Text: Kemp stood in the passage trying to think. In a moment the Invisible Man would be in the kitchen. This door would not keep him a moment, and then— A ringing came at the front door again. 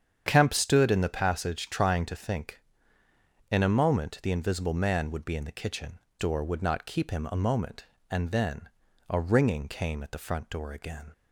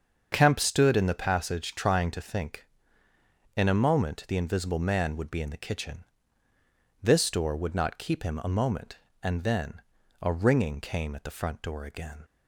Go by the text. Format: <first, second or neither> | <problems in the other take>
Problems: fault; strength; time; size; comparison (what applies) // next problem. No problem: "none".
second | starts louder than the rest; strong; until 1.2 s; 8 dB; also in the second // skips "This"; at 6.0 s